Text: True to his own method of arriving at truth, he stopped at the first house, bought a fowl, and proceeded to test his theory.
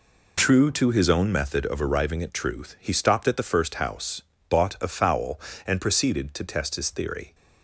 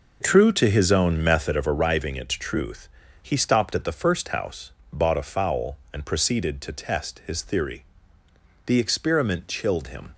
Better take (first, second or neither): first